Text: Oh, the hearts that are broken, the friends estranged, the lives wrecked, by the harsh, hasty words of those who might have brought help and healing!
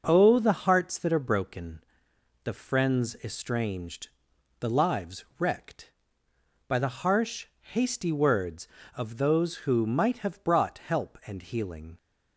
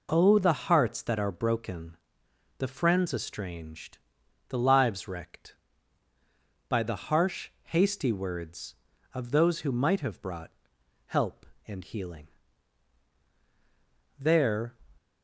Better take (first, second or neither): first